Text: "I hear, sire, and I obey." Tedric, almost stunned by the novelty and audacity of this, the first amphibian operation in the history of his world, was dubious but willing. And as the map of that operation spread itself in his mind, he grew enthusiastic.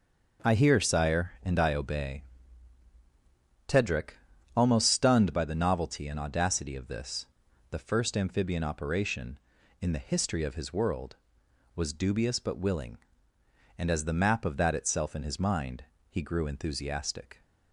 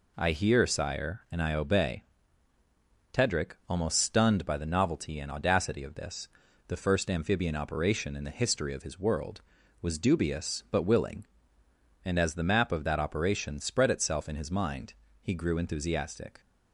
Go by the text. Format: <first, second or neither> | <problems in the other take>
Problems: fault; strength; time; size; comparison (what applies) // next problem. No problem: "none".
second | skips "operation spread"; at 14.7 s